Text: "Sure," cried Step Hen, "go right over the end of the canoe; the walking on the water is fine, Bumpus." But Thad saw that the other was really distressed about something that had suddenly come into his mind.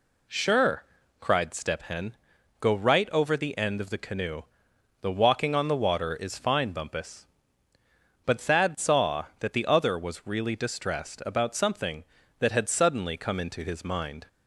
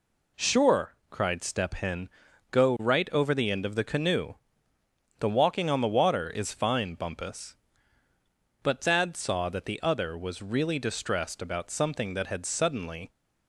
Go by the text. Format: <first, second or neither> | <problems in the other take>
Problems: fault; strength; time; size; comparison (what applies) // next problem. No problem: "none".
first | stops before "come into his mind"; at 13.1 s